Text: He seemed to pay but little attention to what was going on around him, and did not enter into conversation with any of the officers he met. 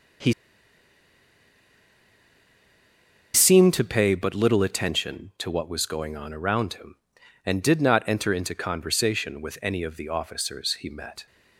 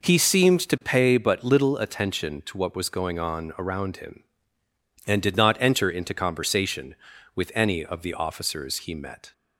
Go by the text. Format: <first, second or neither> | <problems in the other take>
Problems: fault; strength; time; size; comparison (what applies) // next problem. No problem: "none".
second | pauses between "He" and "seemed"; strong; at 0.3 s; 3.0 s long